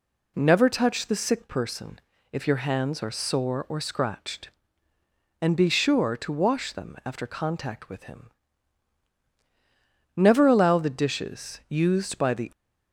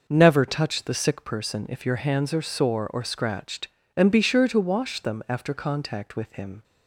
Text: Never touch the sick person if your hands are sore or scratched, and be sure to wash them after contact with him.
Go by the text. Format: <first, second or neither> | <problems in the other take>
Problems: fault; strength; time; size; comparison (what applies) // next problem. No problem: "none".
second | pauses between "person" and "if"; slight; at 2.0 s; 0.32 s long // goes on to say "Never allow the dishes used by the"; strong; from 10.1 s on; 2.3 s long